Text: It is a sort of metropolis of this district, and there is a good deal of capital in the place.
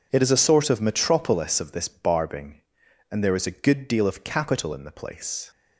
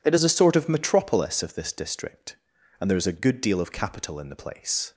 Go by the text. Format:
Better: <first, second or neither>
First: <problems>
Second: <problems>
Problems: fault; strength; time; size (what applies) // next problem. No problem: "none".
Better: second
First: says "barbing" for "district"; at 1.8 s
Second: none